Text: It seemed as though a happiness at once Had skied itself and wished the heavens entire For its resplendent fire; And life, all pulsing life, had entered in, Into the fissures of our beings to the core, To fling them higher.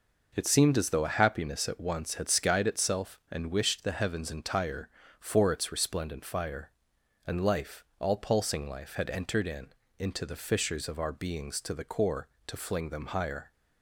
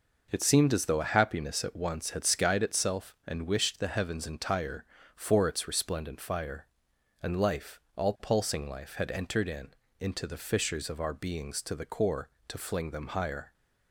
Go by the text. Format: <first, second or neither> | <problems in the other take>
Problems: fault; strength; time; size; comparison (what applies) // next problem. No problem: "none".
neither | none